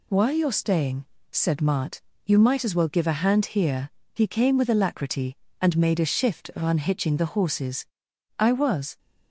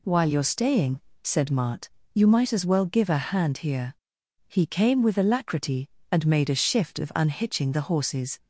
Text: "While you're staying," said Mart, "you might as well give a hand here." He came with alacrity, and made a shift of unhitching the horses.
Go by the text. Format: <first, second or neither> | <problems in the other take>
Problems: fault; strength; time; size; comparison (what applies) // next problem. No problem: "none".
second | goes on to say "I was"; from 8.3 s on; 0.58 s long